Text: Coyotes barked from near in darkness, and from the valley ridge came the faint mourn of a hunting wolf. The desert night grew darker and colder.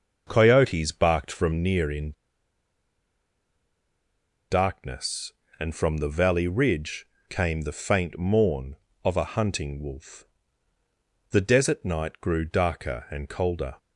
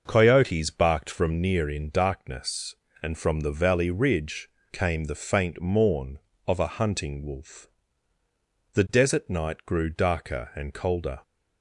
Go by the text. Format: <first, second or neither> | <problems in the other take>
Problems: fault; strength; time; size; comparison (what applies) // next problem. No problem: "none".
second | starts louder than the rest; until 1.2 s; 6.5 dB; also in the second // pauses between "in" and "darkness"; strong; at 2.1 s; 2.3 s long // pauses between "ridge" and "came"; slight; at 7.0 s; 0.22 s long; slight in the second